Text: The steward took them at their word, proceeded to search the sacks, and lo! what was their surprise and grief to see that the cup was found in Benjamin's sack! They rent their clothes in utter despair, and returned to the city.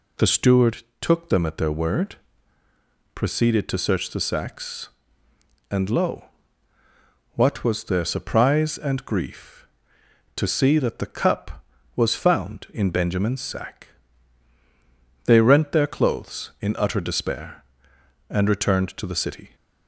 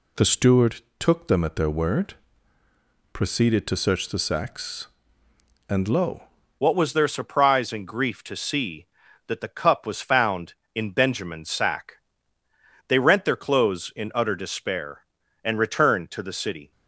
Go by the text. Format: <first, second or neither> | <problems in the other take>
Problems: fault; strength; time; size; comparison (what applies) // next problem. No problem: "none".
first | pauses between "steward" and "took"; slight; at 0.8 s; 0.16 s long; slight in the first // changes voice at "what"; from 6.5 s on; 10.2 s long